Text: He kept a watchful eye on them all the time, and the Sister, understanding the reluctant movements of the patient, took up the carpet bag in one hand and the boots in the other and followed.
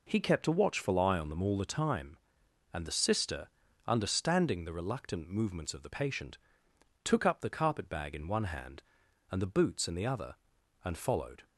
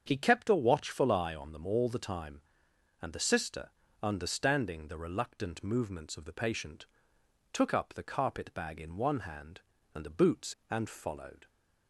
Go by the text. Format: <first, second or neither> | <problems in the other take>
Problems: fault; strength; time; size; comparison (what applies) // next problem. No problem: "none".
first | starts louder than the rest; strong; until 1.0 s; 7 dB // skips "in the other"; at 10.6 s